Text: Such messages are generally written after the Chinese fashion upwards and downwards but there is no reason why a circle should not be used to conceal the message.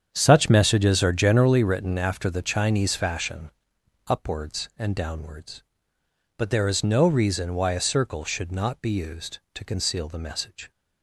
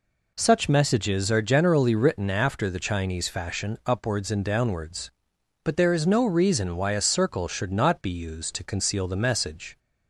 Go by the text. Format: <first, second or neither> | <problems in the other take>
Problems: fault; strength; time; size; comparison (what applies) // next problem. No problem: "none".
second | starts louder than the rest; strong; until 1.7 s; 8 dB // pauses between "fashion" and "upwards"; noticeable; at 3.4 s; 0.58 s long